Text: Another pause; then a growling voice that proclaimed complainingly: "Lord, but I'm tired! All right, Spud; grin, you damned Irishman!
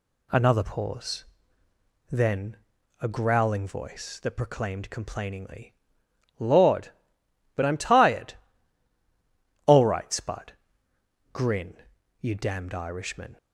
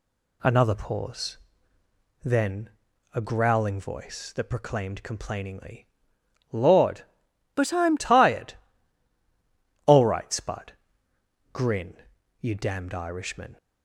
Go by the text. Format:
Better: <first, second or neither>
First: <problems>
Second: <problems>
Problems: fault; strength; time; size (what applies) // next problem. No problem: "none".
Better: first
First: pauses between "then" and "a"; at 2.5 s; 0.42 s long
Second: pauses between "then" and "a"; at 2.7 s; 0.42 s long // changes voice from "but" to "I'm"; from 7.5 to 7.9 s; 0.4 s long